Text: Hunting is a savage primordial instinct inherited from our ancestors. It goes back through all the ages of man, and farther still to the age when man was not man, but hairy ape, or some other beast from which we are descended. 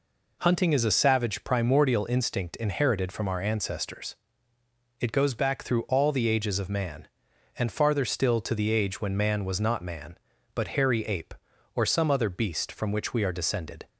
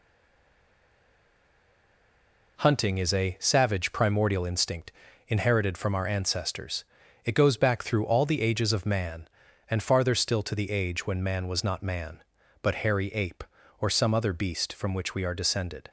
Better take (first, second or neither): first